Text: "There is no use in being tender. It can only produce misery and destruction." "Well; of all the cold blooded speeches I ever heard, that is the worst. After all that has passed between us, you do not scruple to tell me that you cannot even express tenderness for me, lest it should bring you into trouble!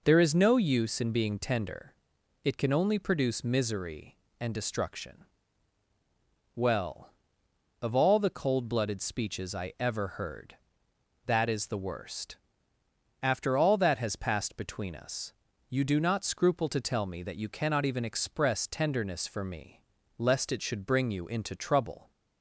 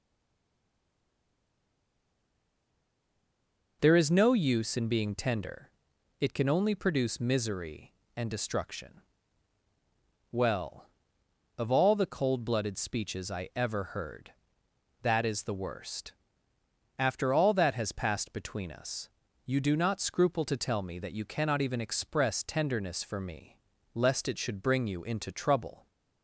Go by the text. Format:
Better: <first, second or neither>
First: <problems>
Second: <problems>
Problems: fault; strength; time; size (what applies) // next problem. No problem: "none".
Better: first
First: none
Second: stays silent before the first word; strong; until 3.8 s; 3.8 s long